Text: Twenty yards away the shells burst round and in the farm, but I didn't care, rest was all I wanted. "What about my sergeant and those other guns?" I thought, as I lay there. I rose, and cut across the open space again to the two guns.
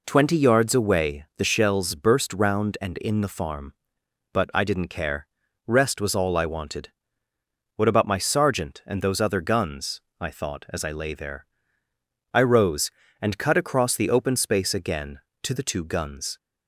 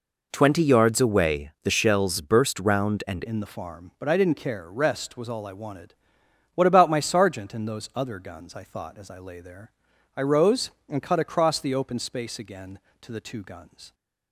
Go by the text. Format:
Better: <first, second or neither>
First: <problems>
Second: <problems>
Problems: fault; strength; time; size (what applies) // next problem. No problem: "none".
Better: first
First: none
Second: changes voice at "in"; from 3.2 s on; 10.7 s long